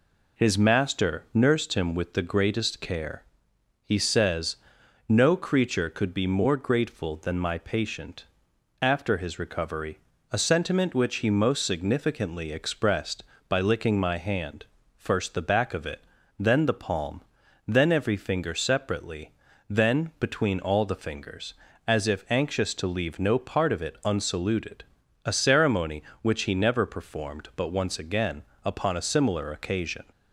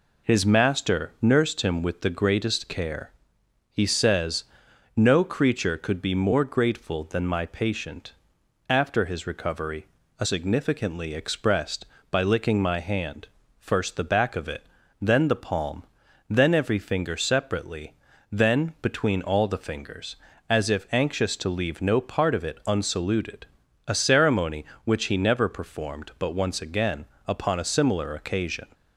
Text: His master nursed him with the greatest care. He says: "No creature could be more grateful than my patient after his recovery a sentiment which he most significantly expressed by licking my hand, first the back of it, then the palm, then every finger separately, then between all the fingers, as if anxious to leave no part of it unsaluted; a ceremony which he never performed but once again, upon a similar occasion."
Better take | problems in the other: first | pauses between "patient" and "after"; noticeable; at 8.1 s; 0.52 s long; noticeable in the first // pauses between "recovery" and "a"; slight; at 9.8 s; 0.34 s long; slight in the first // skips "sentiment which he most"; at 10.2 s

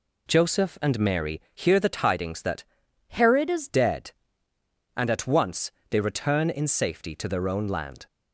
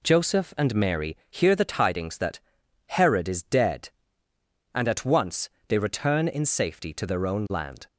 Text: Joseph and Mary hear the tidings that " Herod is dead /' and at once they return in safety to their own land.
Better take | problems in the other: second | changes voice from "Herod" to "is"; from 3.0 to 3.6 s; 0.6 s long // pauses between "once" and "they"; slight; at 5.6 s; 0.20 s long; slight in the second

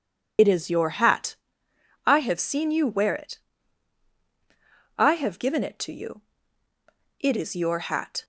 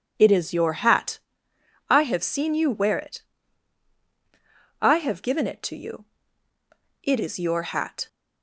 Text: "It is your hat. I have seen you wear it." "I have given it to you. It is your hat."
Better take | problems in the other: second | loses the start of "It"; at 0.3 s; 50 ms

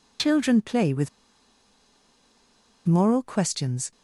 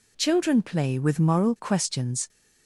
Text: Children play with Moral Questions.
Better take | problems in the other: second | pauses between "with" and "Moral"; strong; at 1.0 s; 1.7 s long

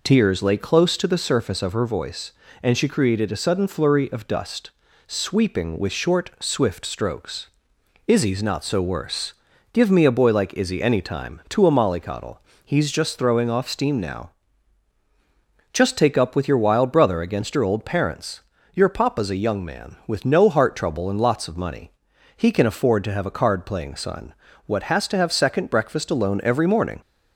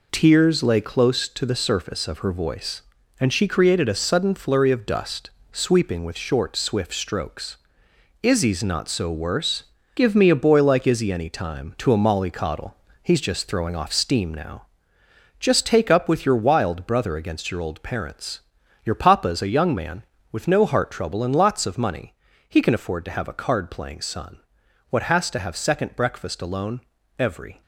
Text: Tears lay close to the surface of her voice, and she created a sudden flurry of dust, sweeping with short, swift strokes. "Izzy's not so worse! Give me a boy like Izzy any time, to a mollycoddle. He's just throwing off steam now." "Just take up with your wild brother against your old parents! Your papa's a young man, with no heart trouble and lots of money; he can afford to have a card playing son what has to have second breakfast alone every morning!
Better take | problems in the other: first | pauses between "son" and "what"; noticeable; at 24.3 s; 0.50 s long; slight in the first // pauses between "alone" and "every"; at 26.7 s; 0.40 s long // stops before "morning"; at 27.6 s

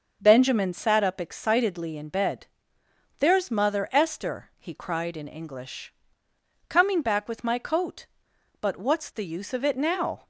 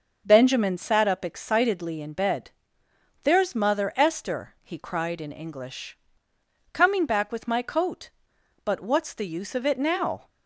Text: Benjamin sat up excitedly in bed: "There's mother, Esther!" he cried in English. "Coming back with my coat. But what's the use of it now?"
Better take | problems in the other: neither | starts louder than the rest; the same in both

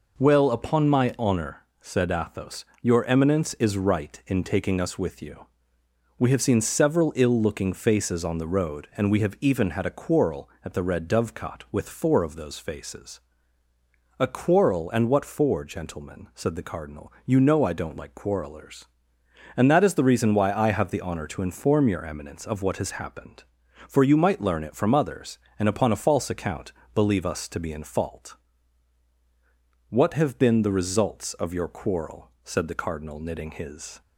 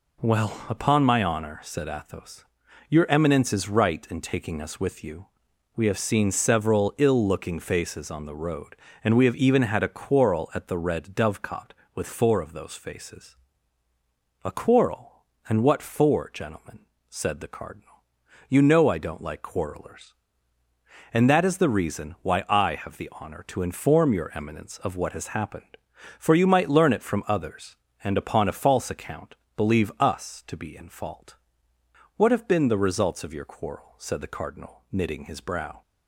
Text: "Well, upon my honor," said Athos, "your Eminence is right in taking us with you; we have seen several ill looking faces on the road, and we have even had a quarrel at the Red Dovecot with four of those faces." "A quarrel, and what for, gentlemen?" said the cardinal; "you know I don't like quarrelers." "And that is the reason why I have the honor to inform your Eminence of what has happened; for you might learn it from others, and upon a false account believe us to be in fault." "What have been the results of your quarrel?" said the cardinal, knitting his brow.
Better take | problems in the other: second | pauses between "account" and "believe"; slight; at 26.7 s; 0.22 s long; slight in the second // stops before "brow"; at 34.0 s

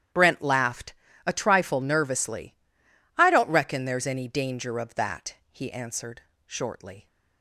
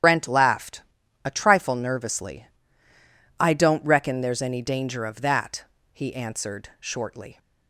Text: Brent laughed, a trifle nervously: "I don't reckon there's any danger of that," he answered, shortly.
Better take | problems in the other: first | loses the start of "Brent"; at 0.0 s; 95 ms // starts louder than the rest; strong; until 1.4 s; 9.5 dB; strong in the first

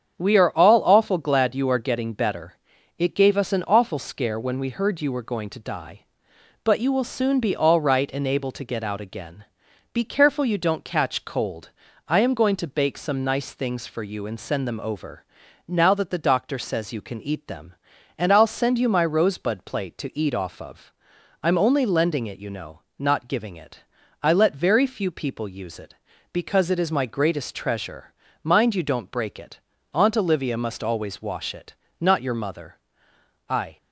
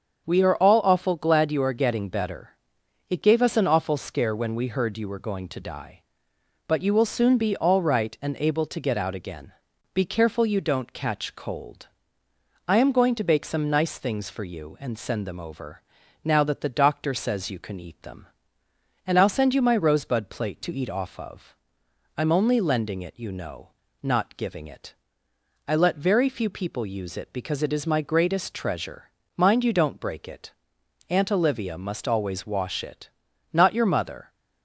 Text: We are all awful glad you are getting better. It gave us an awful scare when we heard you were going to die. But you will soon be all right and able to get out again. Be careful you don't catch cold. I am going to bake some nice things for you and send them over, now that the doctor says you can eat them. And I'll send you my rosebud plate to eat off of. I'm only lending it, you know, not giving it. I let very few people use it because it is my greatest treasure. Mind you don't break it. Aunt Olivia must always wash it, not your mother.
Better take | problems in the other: second | starts louder than the rest; strong; until 1.2 s; 7.5 dB; also in the second // goes on to say "I"; slight; from 33.4 s on; 0.28 s long

